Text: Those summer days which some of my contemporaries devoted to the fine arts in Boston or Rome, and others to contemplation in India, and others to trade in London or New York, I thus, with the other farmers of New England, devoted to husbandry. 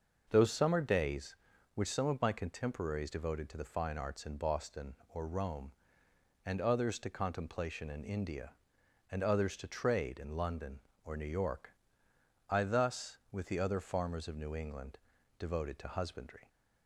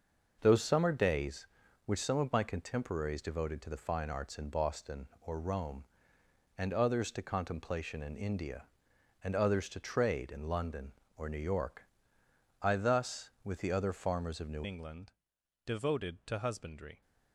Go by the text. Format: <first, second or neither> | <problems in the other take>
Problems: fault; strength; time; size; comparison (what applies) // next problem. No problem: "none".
first | changes voice at "England"; from 14.6 s on; 2.4 s long